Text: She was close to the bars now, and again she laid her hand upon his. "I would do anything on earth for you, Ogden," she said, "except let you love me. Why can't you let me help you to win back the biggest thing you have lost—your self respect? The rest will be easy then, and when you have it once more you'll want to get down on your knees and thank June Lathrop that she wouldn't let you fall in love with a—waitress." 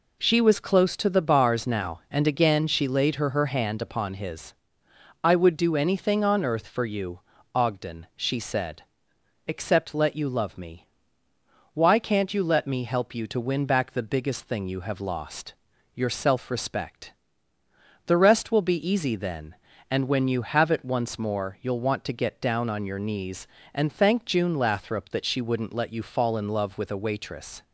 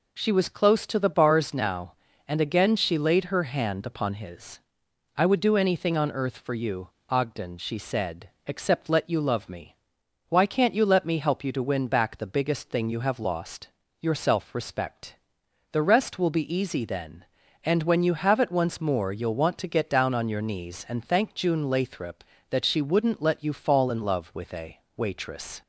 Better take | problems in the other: second | says "her" twice; at 3.2 s

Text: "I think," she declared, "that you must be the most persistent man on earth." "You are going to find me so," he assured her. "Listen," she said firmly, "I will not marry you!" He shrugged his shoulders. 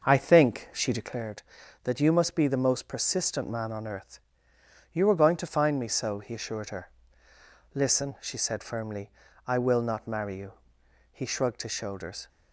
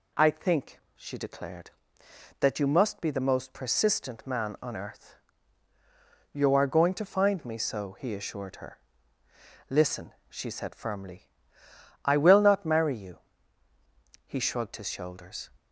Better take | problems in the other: second | starts louder than the rest; noticeable; until 1.2 s; 6 dB

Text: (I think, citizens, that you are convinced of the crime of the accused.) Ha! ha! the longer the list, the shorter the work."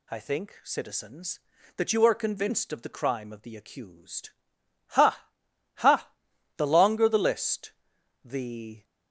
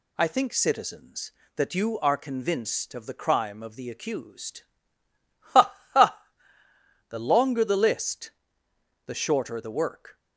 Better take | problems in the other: second | stops before "shorter the work"; at 8.8 s

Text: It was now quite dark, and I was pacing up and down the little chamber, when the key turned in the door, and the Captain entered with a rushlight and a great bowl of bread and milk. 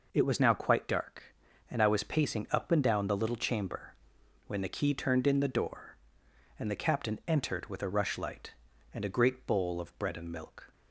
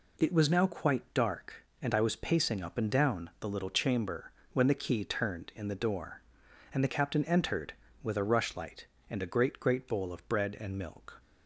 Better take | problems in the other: first | says "great" twice; at 9.5 s

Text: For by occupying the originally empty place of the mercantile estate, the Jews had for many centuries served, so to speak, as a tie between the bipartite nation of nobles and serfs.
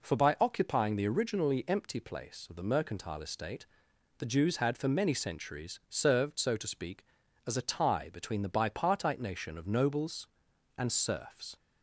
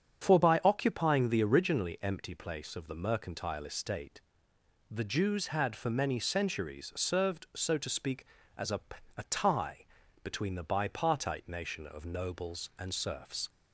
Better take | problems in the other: first | starts louder than the rest; strong; until 1.2 s; 7.5 dB // says "a" twice; at 9.1 s // pauses between "tie" and "between"; at 9.8 s; 0.38 s long

